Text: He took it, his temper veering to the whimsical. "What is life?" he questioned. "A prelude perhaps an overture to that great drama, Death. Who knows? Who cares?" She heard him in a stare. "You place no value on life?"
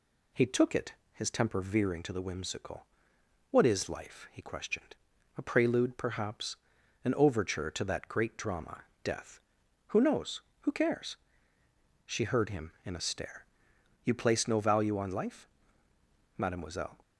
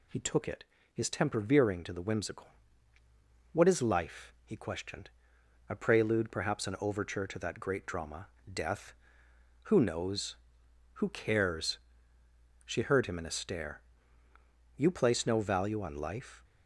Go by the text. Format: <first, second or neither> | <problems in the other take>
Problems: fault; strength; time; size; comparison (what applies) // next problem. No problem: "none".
second | pauses between "perhaps" and "an"; noticeable; at 6.5 s; 0.48 s long // goes on to say "Mademoiselle"; noticeable; from 16.3 s on; 0.62 s long